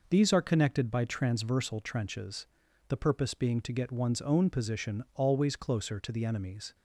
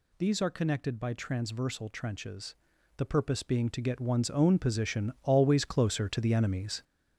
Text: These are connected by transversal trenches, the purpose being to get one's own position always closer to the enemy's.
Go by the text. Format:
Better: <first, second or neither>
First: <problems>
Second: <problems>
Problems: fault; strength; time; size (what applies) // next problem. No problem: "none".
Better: first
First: none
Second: gets louder; noticeable; throughout; 5.5 dB